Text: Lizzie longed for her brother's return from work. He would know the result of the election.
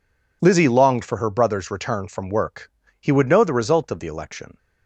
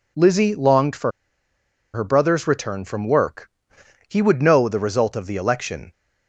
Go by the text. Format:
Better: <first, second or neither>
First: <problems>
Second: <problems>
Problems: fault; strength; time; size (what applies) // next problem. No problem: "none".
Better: first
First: none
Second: pauses between "for" and "her"; noticeable; at 1.1 s; 0.83 s long